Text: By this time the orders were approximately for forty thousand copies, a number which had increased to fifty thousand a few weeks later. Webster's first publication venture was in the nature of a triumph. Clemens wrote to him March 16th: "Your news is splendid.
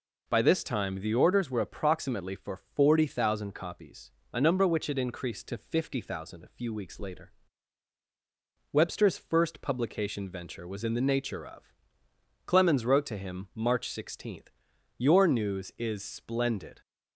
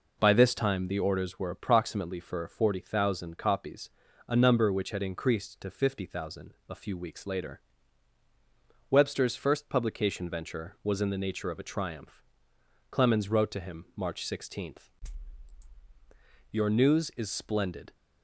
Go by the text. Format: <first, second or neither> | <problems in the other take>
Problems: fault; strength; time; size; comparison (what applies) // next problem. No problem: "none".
second | skips "a triumph"; at 12.0 s